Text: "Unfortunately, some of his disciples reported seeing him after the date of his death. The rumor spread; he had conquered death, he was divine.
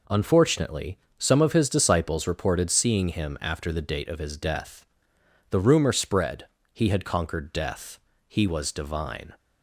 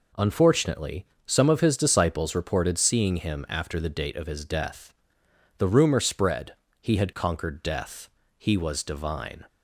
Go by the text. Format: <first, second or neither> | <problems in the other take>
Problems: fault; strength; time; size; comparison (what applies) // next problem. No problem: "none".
neither | none